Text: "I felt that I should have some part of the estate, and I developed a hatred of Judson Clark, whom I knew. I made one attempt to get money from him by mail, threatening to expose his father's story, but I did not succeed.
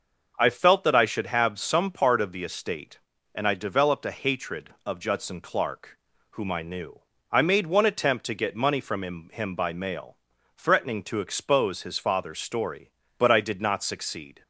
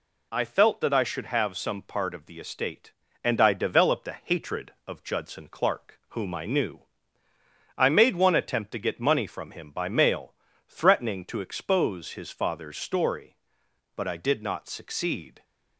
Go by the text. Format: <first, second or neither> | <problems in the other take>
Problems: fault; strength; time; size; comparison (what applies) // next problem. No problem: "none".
second | starts louder than the rest; noticeable; until 1.3 s; 6 dB // says "him" twice; at 9.3 s